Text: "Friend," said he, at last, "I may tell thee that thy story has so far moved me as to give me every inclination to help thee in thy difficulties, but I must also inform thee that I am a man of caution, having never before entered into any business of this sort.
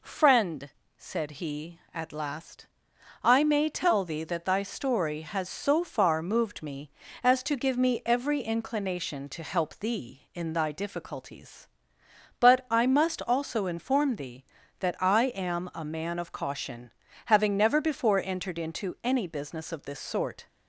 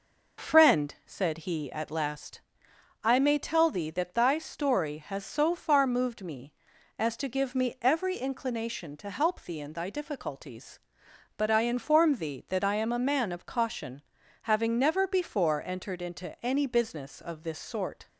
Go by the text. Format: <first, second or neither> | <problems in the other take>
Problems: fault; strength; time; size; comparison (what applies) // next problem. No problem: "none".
first | skips "must also"; at 11.6 s